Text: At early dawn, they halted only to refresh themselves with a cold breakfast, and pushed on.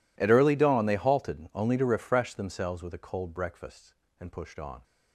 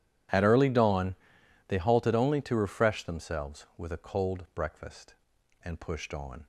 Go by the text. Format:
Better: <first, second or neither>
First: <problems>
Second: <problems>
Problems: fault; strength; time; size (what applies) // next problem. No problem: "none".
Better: neither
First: none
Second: none